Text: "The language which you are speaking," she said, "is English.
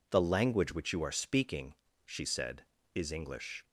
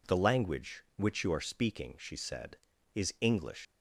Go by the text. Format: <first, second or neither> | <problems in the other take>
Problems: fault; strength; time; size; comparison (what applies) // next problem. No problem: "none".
first | leaves "English" unfinished; at 3.6 s; 135 ms